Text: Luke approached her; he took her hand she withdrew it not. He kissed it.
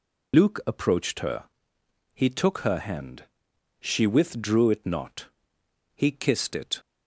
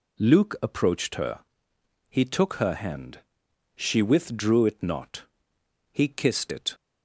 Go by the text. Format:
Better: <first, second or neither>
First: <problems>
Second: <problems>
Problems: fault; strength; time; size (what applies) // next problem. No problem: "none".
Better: second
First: loses the start of "Luke"; at 0.3 s; 105 ms // pauses between "hand" and "she"; noticeable; at 3.2 s; 0.54 s long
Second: pauses between "hand" and "she"; noticeable; at 3.2 s; 0.54 s long